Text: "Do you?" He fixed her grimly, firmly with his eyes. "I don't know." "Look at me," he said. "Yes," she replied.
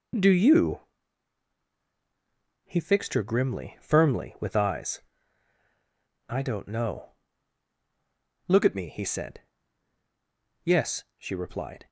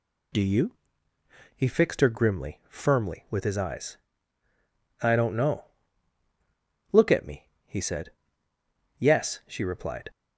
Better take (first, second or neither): second